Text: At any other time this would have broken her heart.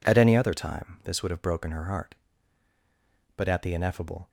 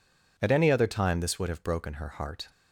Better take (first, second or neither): second